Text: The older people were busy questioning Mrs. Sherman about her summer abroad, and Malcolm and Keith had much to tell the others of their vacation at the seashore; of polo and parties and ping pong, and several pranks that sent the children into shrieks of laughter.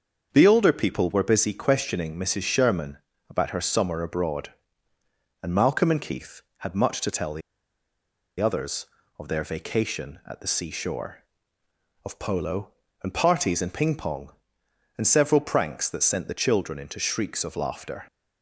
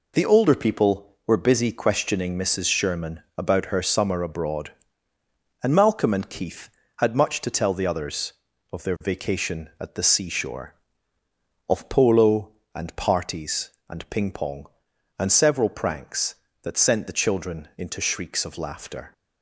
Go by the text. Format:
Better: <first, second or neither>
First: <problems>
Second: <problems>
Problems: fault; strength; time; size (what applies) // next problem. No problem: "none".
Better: second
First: starts louder than the rest; until 1.3 s; 6.5 dB // pauses between "Sherman" and "about"; slight; at 2.9 s; 0.30 s long // pauses between "the" and "others"; at 7.4 s; 0.99 s long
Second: pauses between "Sherman" and "about"; slight; at 3.2 s; 0.16 s long